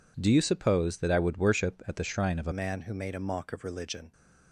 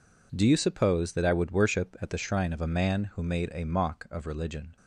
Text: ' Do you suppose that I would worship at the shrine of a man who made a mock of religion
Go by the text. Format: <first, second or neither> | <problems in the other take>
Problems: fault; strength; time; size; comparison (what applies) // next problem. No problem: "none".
second | changes voice at "man"; from 2.5 s on; 1.6 s long